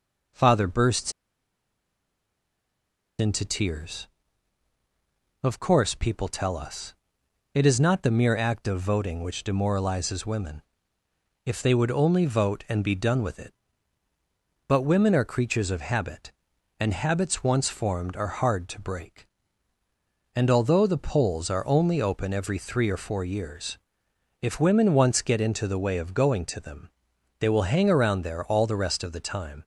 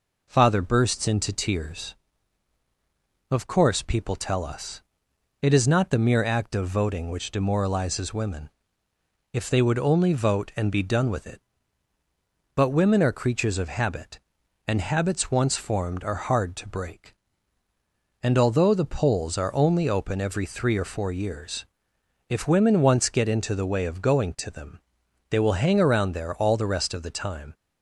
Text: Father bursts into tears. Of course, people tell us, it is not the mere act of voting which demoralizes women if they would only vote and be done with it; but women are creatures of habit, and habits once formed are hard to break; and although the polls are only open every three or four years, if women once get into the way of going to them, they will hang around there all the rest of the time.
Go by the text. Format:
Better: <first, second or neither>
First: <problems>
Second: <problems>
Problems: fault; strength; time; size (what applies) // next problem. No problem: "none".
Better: second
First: pauses between "bursts" and "into"; strong; at 1.1 s; 2.0 s long // pauses between "women" and "if"; noticeable; at 10.6 s; 0.80 s long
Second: pauses between "women" and "if"; noticeable; at 8.5 s; 0.80 s long